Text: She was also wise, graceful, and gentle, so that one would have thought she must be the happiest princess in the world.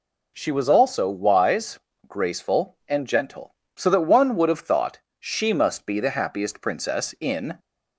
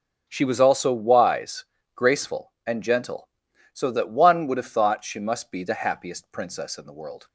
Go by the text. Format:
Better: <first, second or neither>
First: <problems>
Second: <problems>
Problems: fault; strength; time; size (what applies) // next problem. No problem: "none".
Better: second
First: pauses between "thought" and "she"; slight; at 4.9 s; 0.22 s long // stops before "the world"; at 7.5 s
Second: none